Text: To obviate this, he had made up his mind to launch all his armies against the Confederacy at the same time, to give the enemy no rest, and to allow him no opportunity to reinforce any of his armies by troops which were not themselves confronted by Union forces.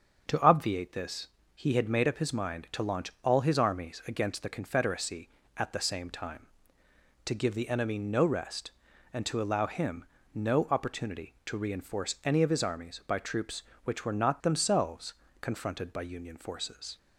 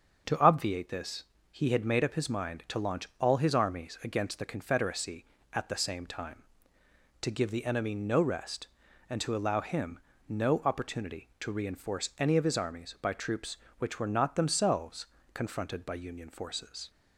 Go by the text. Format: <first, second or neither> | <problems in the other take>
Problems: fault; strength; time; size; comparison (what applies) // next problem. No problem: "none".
neither | starts louder than the rest; the same in both // pauses between "him" and "no"; slight; the same in both // pauses between "themselves" and "confronted"; slight; the same in both